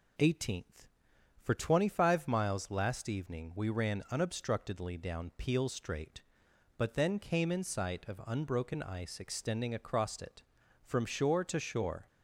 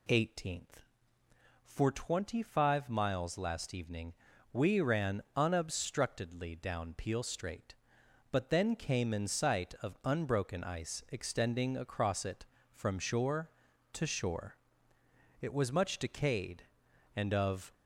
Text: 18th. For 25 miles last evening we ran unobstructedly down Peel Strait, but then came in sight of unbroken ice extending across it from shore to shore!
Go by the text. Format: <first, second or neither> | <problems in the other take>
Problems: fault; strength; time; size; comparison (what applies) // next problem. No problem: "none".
first | pauses between "evening" and "we"; at 4.1 s; 0.40 s long // goes on to say "It was much decayed and of"; strong; from 15.4 s on; 2.3 s long